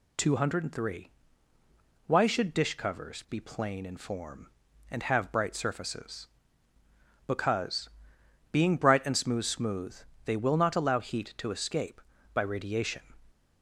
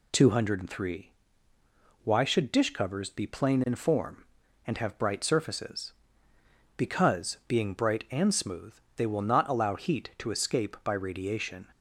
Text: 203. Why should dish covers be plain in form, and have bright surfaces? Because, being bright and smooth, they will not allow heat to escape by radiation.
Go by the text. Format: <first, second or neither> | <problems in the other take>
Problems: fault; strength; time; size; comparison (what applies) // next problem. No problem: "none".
second | says "smooth" twice; at 9.4 s